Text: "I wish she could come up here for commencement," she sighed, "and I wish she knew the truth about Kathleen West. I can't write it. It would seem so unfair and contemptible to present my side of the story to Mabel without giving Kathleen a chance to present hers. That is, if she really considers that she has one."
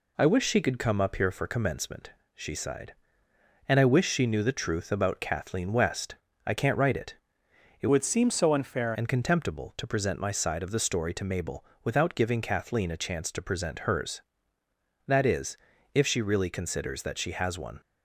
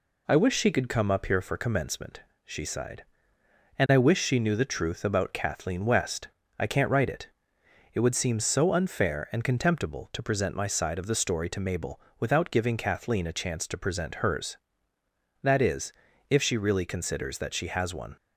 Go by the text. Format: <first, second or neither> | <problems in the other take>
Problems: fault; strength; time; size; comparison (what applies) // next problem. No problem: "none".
second | changes voice from "would" to "unfair"; from 7.8 to 8.9 s; 1.1 s long // pauses between "Mabel" and "without"; slight; at 11.6 s; 0.18 s long; slight in the second